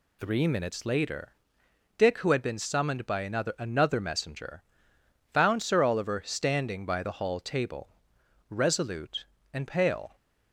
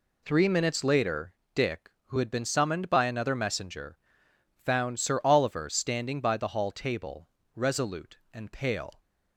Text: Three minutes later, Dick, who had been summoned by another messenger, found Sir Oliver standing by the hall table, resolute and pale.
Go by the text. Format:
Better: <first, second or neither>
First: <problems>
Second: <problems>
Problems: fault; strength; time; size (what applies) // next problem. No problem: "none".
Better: second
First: says "another" twice; at 3.5 s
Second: none